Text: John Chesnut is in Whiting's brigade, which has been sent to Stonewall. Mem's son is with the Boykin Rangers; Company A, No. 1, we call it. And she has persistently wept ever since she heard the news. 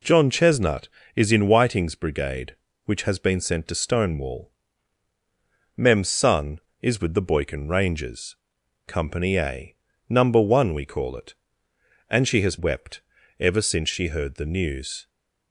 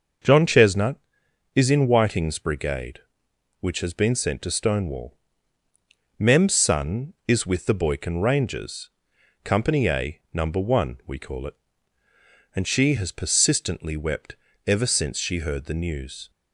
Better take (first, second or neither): second